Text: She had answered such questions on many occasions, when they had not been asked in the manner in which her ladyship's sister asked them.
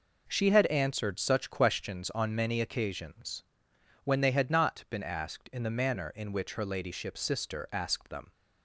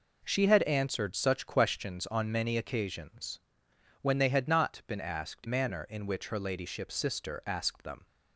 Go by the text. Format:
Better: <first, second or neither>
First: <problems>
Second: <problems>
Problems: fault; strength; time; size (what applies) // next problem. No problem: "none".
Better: first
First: none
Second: skips "in the"; at 5.4 s